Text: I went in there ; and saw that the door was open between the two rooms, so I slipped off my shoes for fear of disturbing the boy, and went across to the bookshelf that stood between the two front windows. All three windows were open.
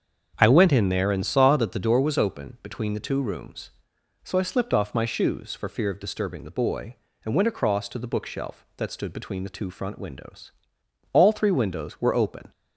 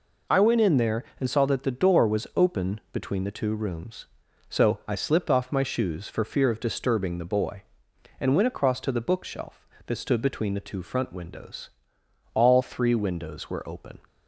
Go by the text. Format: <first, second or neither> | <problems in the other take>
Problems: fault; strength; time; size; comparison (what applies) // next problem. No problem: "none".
second | starts louder than the rest; until 1.9 s; 7 dB